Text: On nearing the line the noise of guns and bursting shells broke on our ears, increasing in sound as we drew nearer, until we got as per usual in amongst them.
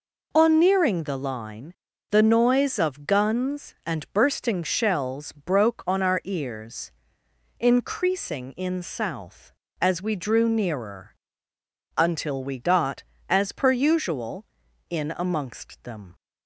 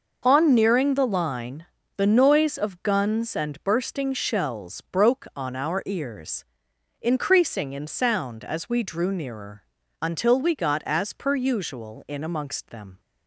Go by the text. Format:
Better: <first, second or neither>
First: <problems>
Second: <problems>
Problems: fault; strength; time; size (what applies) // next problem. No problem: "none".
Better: second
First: pauses between "line" and "the"; at 1.7 s; 0.38 s long // says "south" for "sound"; at 8.8 s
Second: pauses between "line" and "the"; slight; at 1.6 s; 0.32 s long